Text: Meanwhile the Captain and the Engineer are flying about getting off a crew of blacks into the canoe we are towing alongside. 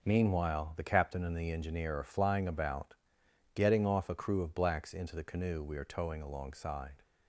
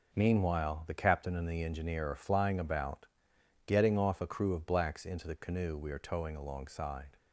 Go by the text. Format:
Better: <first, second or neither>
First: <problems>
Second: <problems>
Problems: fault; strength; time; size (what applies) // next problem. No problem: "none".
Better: neither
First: pauses between "about" and "getting"; noticeable; at 2.9 s; 0.60 s long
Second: pauses between "about" and "getting"; noticeable; at 3.0 s; 0.60 s long